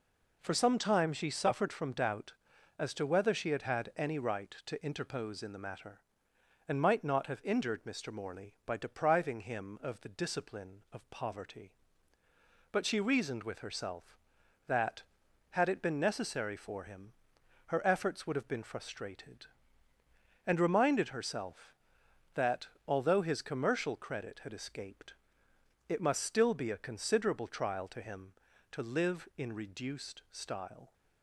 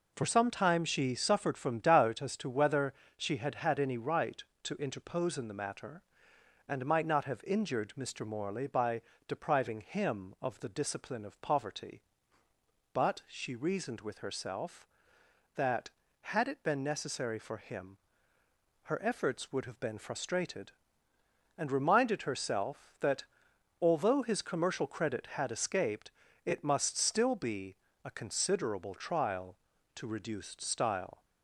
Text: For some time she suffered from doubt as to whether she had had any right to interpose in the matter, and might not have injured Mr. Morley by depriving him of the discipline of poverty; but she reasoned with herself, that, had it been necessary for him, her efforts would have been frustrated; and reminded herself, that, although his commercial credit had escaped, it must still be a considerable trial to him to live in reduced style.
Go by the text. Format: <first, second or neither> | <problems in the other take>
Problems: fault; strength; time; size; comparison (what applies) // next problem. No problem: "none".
first | pauses between "whether" and "she"; slight; at 2.9 s; 0.24 s long // pauses between "by" and "depriving"; slight; at 9.0 s; 0.24 s long // pauses between "be" and "a"; slight; at 27.7 s; 0.30 s long // skips "him to live in"; at 30.0 s